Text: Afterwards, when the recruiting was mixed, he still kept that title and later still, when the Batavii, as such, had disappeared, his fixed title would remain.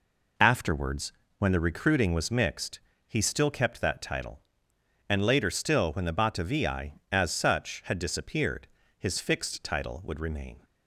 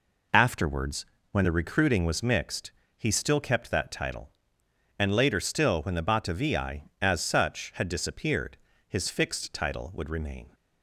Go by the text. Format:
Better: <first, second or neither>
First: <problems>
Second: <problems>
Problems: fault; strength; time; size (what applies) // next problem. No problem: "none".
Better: neither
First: none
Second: none